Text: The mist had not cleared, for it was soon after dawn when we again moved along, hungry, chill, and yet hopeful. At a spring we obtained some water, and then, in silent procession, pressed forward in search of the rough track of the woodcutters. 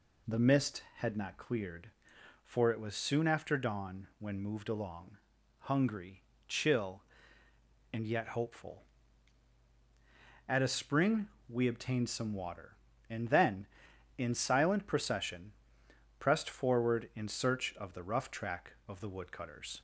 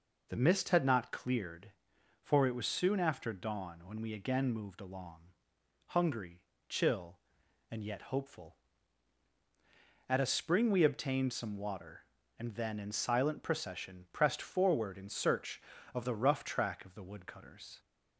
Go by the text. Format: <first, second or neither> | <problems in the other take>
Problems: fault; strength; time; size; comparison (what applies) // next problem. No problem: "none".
second | skips "we again"; at 4.4 s // pauses between "spring" and "we"; slight; at 11.2 s; 0.20 s long